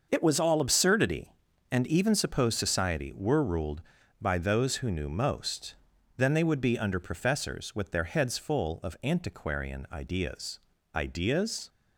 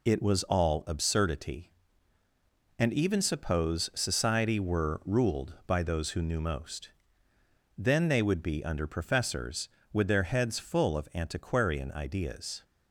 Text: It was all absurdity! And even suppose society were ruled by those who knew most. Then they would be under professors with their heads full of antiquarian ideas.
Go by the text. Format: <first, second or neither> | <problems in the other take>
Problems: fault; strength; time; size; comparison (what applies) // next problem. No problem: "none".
second | starts louder than the rest; until 1.1 s; 6.5 dB // says "ideas" twice; at 10.9 s